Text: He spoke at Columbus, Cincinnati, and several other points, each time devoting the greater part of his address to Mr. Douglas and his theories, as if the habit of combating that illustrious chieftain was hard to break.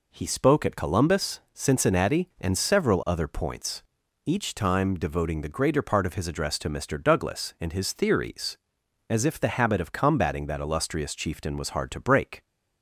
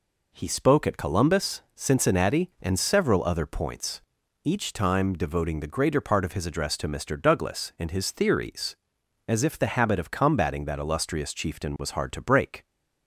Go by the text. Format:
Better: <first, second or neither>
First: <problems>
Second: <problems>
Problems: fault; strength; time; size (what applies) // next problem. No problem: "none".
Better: neither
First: none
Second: none